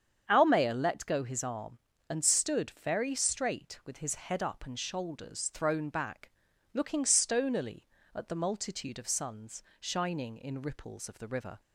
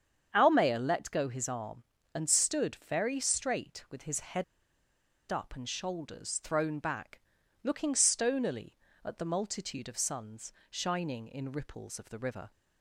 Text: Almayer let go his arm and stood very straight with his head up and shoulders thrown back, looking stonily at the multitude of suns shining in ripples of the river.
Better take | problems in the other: first | starts louder than the rest; strong; until 1.3 s; 7.5 dB; strong in the first // pauses between "head" and "up"; noticeable; at 4.4 s; 0.86 s long // pauses between "suns" and "shining"; slight; at 10.5 s; 0.20 s long; slight in the first

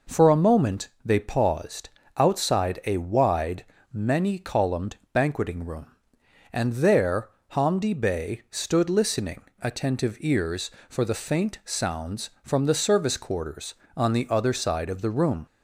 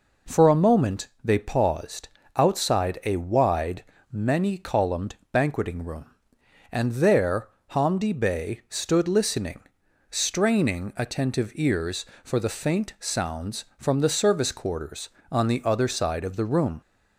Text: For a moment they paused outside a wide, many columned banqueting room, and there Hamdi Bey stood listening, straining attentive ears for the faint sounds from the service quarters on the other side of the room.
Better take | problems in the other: second | pauses between "moment" and "they"; slight; at 0.8 s; 0.16 s long; slight in the second // pauses between "paused" and "outside"; slight; at 1.8 s; 0.26 s long; slight in the second // pauses between "columned" and "banqueting"; slight; at 4.9 s; 0.16 s long; slight in the second // pauses between "there" and "Hamdi"; slight; at 7.2 s; 0.22 s long; slight in the second // skips "straining"; at 9.5 s

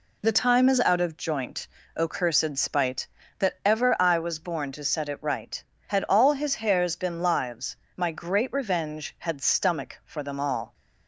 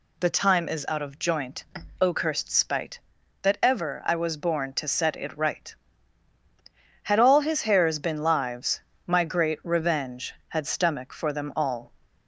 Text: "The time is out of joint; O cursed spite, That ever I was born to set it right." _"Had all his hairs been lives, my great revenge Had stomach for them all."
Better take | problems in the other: neither | none

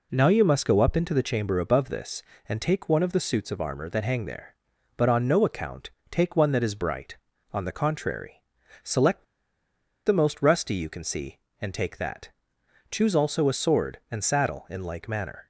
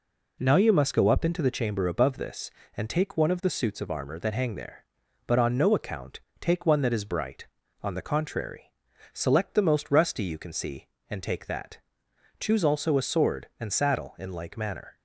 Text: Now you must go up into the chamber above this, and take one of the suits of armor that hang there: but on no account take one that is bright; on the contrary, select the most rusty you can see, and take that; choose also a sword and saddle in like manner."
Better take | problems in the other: second | pauses between "account" and "take"; slight; at 5.9 s; 0.18 s long; slight in the second // pauses between "select" and "the"; noticeable; at 9.2 s; 0.82 s long

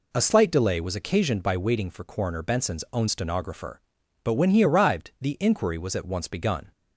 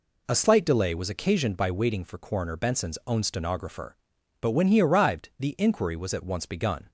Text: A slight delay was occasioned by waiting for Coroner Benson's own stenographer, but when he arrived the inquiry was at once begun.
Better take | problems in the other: neither | none

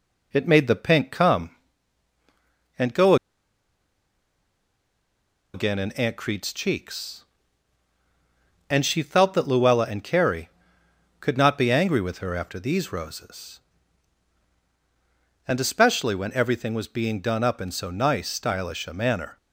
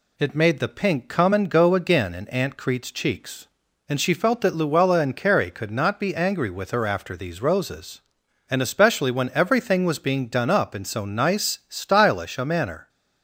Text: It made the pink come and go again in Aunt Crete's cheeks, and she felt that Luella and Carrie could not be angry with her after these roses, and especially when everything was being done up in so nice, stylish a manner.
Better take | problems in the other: second | pauses between "go" and "again"; strong; at 3.1 s; 2.3 s long

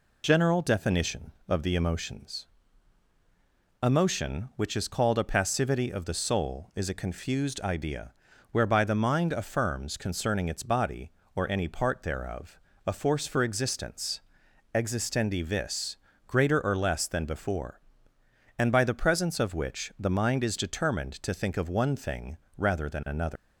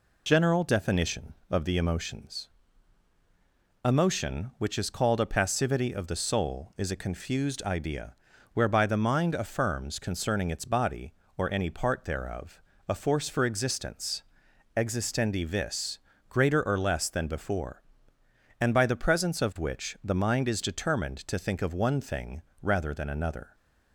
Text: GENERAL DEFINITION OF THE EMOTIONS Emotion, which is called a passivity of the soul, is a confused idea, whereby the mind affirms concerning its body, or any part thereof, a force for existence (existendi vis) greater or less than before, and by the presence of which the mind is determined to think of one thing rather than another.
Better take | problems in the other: second | pauses between "EMOTIONS" and "Emotion"; strong; at 2.4 s; 1.3 s long; strong in the second // pauses between "thing" and "rather"; slight; at 22.3 s; 0.22 s long; slight in the second // leaves "another" unfinished; at 23.3 s; 180 ms

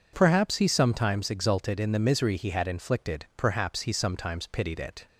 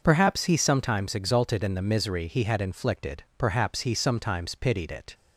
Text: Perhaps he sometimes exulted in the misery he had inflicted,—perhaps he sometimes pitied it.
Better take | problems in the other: neither | none

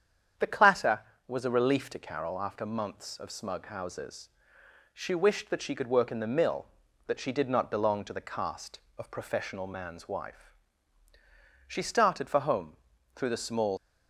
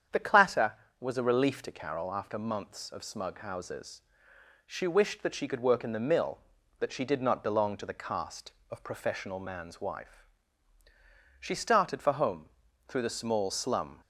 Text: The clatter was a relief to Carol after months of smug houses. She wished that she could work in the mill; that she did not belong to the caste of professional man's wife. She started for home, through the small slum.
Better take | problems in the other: second | starts louder than the rest; strong; until 1.6 s; 8 dB; strong in the second // stops before "slum"; at 13.7 s

